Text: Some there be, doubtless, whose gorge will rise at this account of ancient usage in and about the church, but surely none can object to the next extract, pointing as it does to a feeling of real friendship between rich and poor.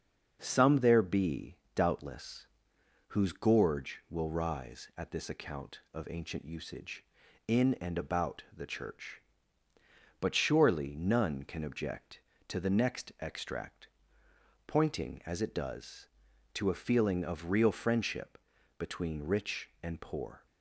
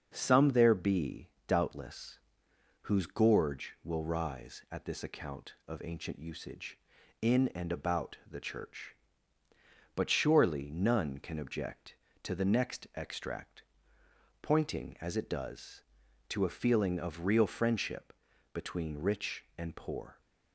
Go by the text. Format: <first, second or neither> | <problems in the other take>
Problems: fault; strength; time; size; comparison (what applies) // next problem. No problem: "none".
neither | starts louder than the rest; the same in both // pauses between "friendship" and "between"; the same in both